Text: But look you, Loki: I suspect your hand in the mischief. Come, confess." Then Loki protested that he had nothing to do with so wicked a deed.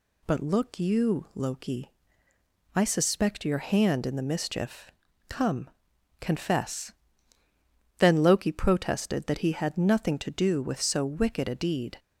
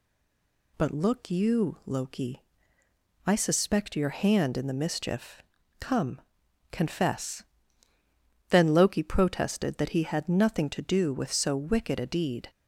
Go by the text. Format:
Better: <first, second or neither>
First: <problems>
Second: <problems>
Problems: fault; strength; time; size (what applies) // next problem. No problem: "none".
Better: first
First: none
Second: stays silent before the first word; slight; until 0.7 s; 0.7 s long